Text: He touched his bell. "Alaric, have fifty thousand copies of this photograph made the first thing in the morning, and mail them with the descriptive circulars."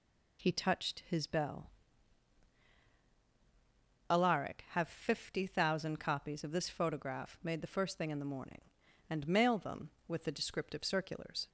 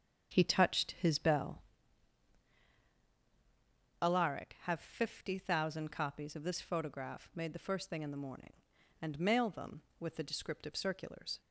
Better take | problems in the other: first | starts louder than the rest; strong; until 1.7 s; 8 dB

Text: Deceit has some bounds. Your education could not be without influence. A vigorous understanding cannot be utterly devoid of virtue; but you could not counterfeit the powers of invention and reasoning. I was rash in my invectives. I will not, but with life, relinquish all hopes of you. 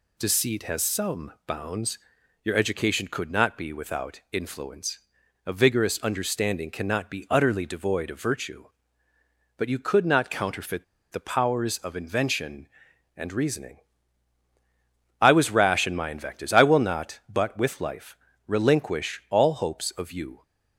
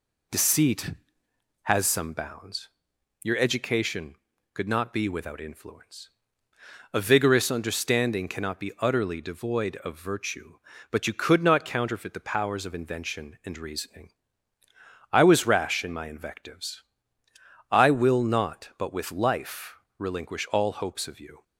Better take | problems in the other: second | pauses between "counterfeit" and "the"; slight; at 10.8 s; 0.27 s long

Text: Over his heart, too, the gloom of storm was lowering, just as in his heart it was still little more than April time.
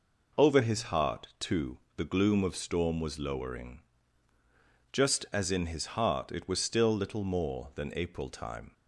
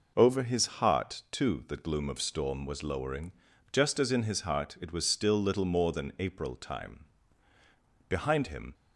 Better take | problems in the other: first | goes on to say "Behind him"; noticeable; from 8.0 s on; 0.66 s long

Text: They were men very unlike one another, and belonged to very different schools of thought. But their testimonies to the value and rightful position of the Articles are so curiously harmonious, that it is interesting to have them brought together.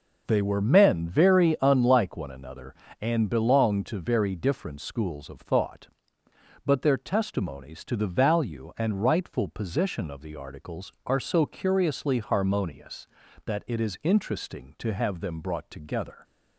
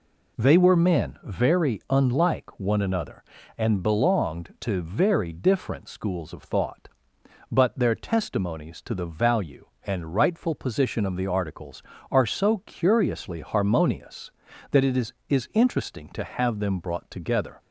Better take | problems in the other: first | says "is" twice; at 15.2 s

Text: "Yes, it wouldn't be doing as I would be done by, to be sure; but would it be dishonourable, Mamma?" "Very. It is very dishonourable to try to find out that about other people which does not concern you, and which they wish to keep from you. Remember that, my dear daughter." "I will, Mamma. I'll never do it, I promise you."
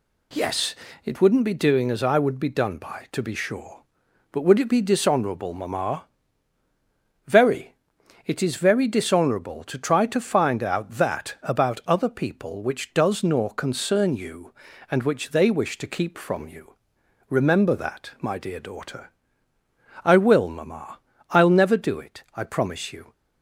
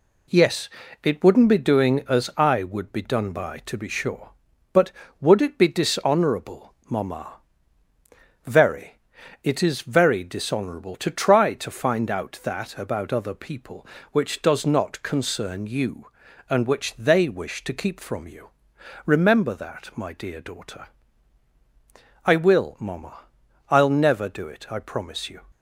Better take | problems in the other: second | says "nor" for "not"; at 13.2 s

